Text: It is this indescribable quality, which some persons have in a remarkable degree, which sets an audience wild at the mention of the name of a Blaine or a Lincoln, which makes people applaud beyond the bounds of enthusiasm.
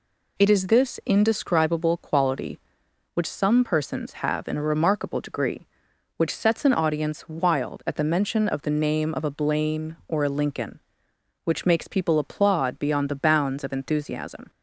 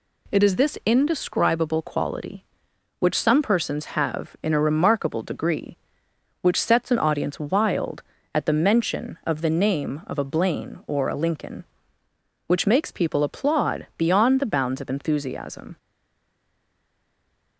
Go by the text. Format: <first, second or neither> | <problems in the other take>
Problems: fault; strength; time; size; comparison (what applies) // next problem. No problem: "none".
first | stays silent after the last word; noticeable; from 15.7 s on; 1.8 s long